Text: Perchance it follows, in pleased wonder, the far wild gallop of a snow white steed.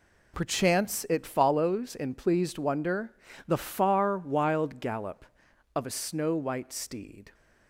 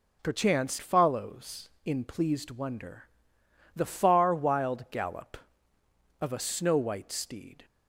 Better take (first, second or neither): first